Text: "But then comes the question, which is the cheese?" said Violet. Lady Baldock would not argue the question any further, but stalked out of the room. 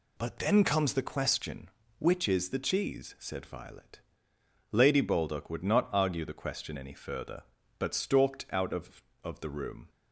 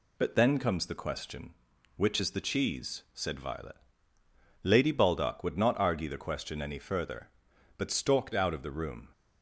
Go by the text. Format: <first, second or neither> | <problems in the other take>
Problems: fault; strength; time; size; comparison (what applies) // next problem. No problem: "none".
second | says "of" twice; at 9.2 s